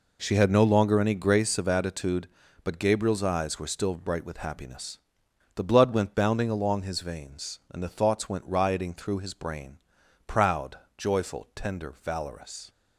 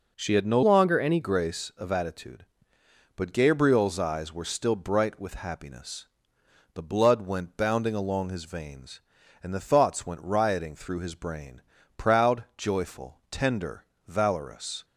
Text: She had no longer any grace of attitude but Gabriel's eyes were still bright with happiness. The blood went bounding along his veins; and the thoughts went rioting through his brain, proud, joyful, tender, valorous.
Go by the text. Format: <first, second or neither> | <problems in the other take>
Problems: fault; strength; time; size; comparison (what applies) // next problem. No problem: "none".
first | changes voice from "longer" to "any"; from 0.6 to 1.1 s; 0.5 s long